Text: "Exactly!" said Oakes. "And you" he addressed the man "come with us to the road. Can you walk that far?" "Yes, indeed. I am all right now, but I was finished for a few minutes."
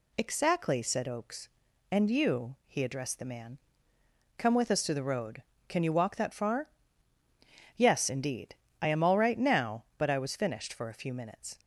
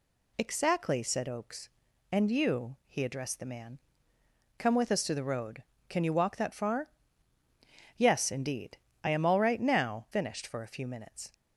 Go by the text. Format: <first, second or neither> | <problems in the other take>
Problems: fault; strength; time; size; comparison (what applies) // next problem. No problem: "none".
first | pauses between "man" and "come"; noticeable; at 3.7 s; 0.80 s long; noticeable in the first // skips "but I was"; at 10.0 s